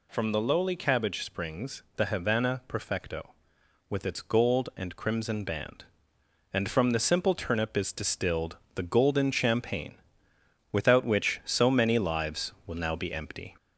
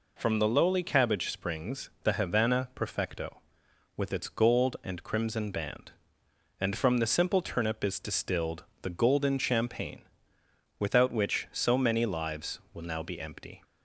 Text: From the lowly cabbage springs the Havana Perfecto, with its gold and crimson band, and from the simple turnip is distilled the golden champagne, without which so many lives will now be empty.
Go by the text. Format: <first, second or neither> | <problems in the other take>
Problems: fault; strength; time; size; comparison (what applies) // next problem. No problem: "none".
second | gets louder; throughout; 3.5 dB // pauses between "distilled" and "the"; slight; at 8.5 s; 0.18 s long; slight in the second